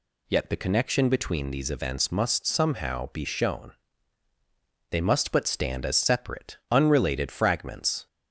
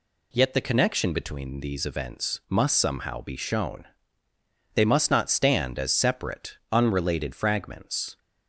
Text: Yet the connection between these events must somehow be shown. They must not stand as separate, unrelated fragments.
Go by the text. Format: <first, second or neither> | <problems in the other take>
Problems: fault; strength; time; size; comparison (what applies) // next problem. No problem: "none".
second | says "but" for "not"; at 5.3 s